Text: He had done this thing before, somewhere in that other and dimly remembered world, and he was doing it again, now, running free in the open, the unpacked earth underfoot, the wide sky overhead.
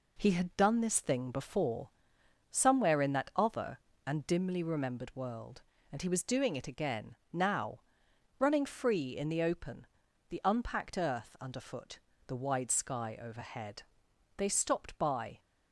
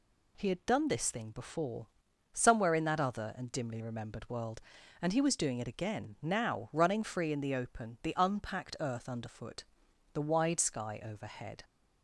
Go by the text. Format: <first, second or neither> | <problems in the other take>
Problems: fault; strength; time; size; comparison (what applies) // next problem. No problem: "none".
second | goes on to say "They stopped by"; noticeable; from 14.3 s on; 1.0 s long